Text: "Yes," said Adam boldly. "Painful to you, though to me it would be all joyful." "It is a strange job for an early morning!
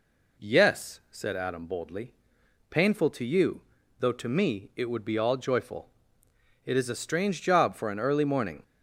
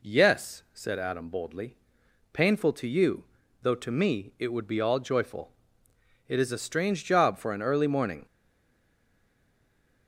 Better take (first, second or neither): first